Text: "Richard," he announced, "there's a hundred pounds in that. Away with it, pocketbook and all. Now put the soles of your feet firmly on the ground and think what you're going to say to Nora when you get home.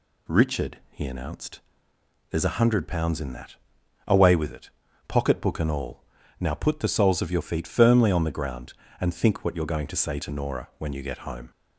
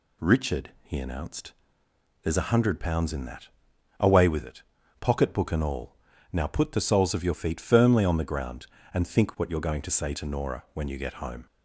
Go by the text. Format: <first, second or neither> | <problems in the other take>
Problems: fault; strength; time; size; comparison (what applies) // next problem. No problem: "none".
neither | none